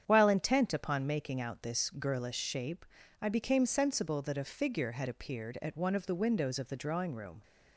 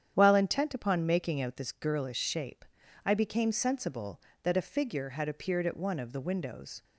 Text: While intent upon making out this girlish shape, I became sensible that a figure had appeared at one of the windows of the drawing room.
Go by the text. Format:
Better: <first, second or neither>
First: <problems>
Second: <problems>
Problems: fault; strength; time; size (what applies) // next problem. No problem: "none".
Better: first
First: starts louder than the rest; strong; until 1.0 s; 8.5 dB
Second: starts louder than the rest; strong; until 1.1 s; 9 dB // stops before "of the drawing room"; at 6.8 s